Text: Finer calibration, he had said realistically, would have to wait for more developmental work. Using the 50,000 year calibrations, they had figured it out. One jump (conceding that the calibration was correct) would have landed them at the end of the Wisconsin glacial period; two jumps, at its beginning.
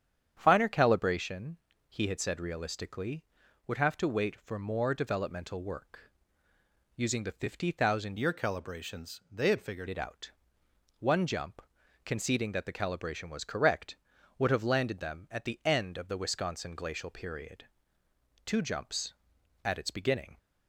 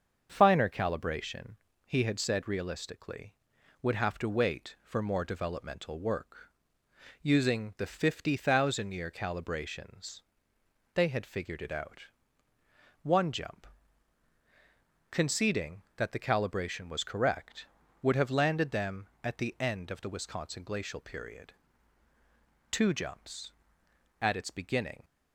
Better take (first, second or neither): second